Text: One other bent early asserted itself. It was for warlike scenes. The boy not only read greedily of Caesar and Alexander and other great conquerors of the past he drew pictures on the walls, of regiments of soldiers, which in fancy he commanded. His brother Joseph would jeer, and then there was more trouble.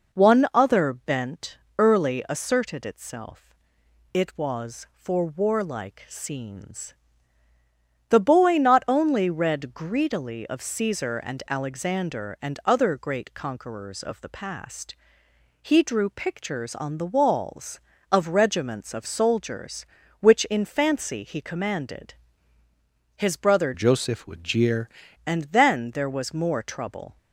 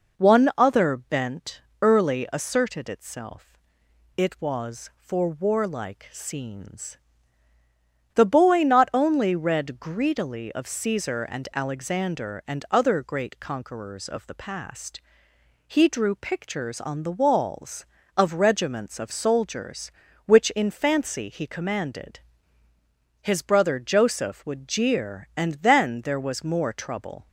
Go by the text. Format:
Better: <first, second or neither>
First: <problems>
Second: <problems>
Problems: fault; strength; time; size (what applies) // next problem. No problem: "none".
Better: second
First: pauses between "bent" and "early"; slight; at 1.5 s; 0.22 s long // pauses between "past" and "he"; noticeable; at 14.9 s; 0.68 s long // changes voice from "Joseph" to "jeer"; from 23.7 to 24.9 s; 1.2 s long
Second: pauses between "bent" and "early"; slight; at 1.5 s; 0.22 s long // pauses between "past" and "he"; noticeable; at 15.0 s; 0.68 s long